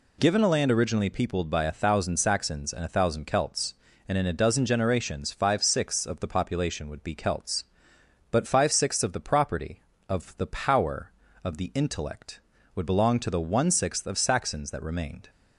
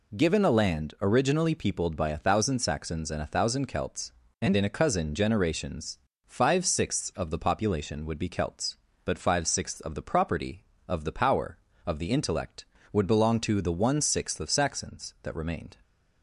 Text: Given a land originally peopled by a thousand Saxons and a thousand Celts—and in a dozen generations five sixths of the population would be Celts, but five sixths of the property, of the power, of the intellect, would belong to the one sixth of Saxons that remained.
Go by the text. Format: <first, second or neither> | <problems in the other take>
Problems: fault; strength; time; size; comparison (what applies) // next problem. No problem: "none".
first | says "cousin" for "dozen"; at 4.6 s // pauses between "generations" and "five"; slight; at 5.9 s; 0.28 s long